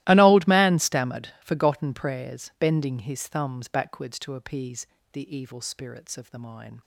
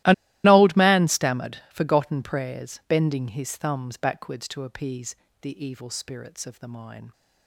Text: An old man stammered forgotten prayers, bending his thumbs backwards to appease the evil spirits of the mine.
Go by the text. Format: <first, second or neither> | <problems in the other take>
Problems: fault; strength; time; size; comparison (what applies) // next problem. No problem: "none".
first | starts louder than the rest; strong; until 1.3 s; 16 dB; strong in the first // pauses between "An" and "old"; slight; at 0.1 s; 0.31 s long // pauses between "appease" and "the"; slight; at 5.1 s; 0.26 s long; slight in the first